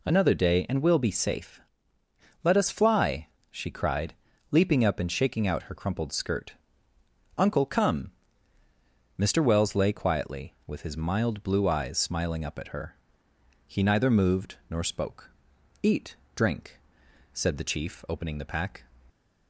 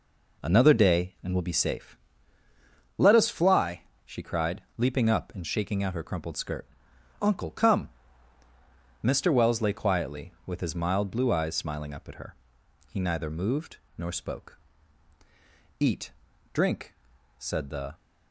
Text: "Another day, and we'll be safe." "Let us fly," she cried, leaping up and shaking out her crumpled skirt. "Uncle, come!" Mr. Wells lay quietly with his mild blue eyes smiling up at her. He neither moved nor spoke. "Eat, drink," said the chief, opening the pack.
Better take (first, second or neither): first